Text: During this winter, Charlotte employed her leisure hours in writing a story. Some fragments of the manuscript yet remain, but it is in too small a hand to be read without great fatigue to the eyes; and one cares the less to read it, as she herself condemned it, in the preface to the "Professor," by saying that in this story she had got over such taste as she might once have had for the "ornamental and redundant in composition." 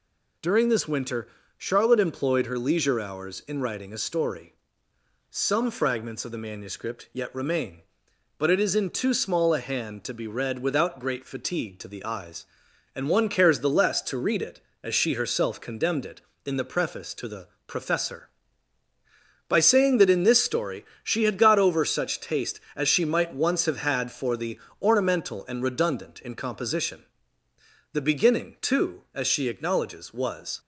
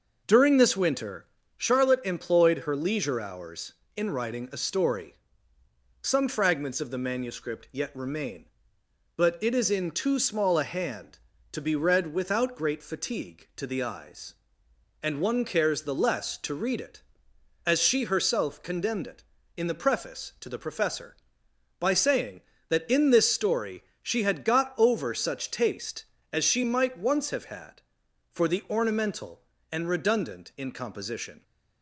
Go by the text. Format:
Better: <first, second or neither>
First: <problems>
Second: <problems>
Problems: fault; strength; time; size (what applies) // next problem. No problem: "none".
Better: second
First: pauses between "the" and "Professor"; slight; at 17.4 s; 0.18 s long // pauses between "story" and "she"; slight; at 20.8 s; 0.18 s long // pauses between "the" and "ornamental"; slight; at 24.5 s; 0.22 s long // goes on to say "The beginning too as she acknowledges was"; strong; from 27.9 s on; 2.6 s long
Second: pauses between "story" and "she"; slight; at 23.8 s; 0.18 s long